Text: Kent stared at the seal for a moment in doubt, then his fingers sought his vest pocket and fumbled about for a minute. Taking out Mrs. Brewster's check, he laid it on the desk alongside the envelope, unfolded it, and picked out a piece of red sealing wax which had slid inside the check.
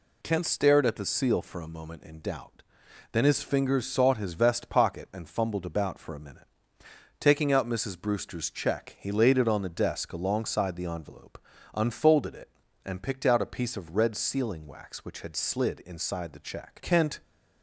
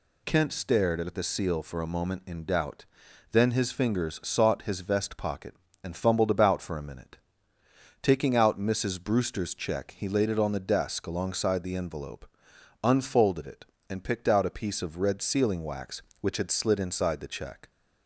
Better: second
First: goes on to say "Kent"; slight; from 16.8 s on; 0.38 s long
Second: none

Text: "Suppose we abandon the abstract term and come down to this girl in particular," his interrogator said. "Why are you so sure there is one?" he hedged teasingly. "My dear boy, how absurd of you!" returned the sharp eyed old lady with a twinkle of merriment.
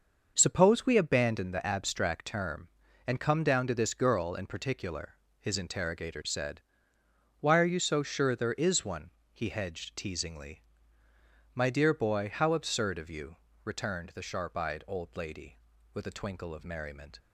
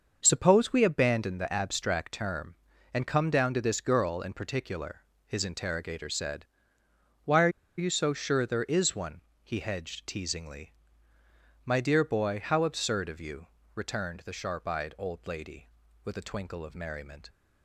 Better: first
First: starts louder than the rest; until 1.3 s; 6.5 dB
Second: starts louder than the rest; until 1.2 s; 6.5 dB // pauses between "are" and "you"; slight; at 7.4 s; 0.29 s long

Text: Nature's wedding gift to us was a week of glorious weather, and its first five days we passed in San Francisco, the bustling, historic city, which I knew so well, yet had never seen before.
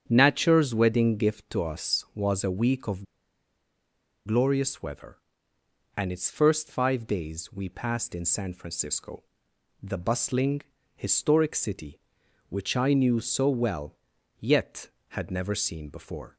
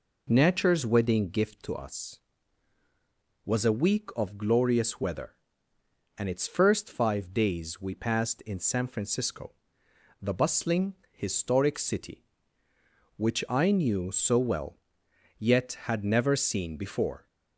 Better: second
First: starts louder than the rest; strong; until 1.0 s; 8.5 dB // pauses between "of" and "glorious"; at 3.0 s; 1.2 s long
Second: none

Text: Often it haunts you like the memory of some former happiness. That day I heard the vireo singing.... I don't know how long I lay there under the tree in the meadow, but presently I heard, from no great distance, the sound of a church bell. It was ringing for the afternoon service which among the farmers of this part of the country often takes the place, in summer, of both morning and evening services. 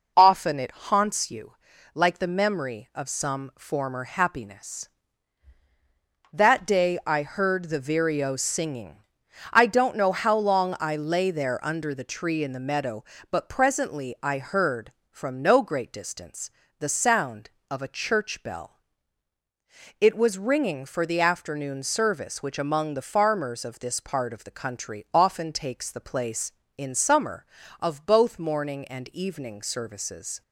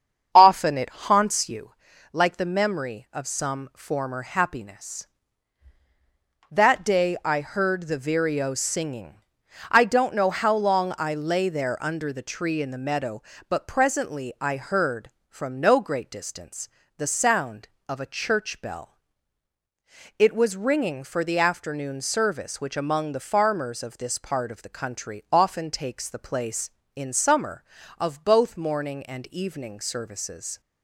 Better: first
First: pauses between "you" and "like"; at 1.5 s; 0.40 s long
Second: starts louder than the rest; strong; until 1.7 s; 7.5 dB // pauses between "you" and "like"; at 1.7 s; 0.40 s long

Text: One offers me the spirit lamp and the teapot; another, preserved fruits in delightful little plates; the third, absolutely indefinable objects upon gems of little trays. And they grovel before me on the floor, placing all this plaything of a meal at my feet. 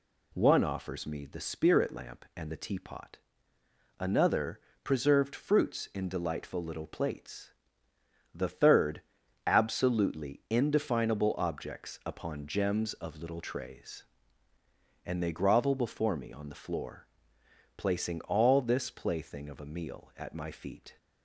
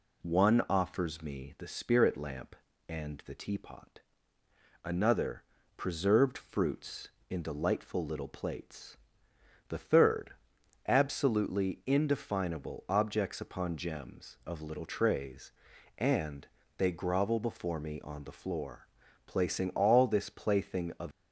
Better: first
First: none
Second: pauses between "And" and "they"; slight; at 16.4 s; 0.32 s long // stops before "a meal at my feet"; at 21.1 s

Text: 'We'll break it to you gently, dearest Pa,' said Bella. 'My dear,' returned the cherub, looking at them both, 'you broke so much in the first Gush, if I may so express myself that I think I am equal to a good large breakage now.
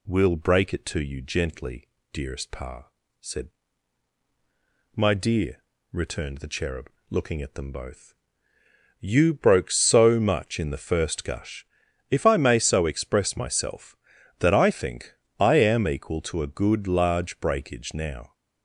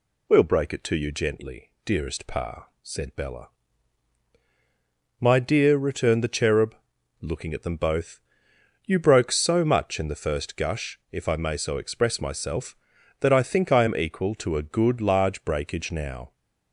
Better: second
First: skips "Bella"; at 4.2 s // pauses between "think" and "I"; slight; at 15.1 s; 0.26 s long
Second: none

